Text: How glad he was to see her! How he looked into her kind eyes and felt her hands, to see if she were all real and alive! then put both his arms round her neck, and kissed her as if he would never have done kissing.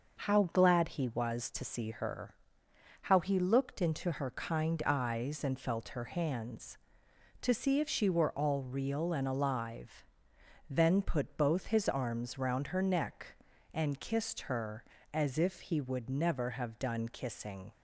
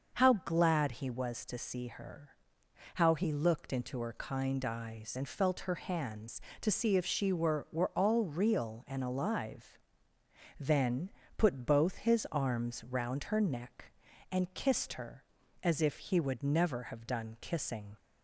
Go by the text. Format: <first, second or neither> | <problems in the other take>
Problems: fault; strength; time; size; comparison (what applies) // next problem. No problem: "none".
first | starts louder than the rest; until 1.2 s; 6 dB // says "were" twice; at 7.7 s // pauses between "then" and "put"; slight; at 11.0 s; 0.28 s long